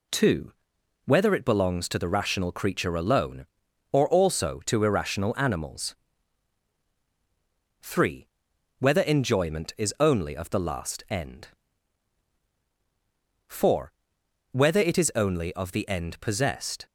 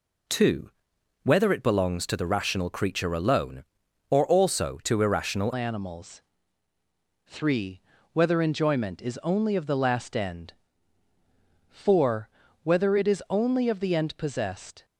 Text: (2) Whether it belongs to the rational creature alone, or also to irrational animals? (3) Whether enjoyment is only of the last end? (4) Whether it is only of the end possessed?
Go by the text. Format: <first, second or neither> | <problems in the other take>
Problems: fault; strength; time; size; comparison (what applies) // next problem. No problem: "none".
first | changes voice at "animals"; from 5.5 s on; 9.3 s long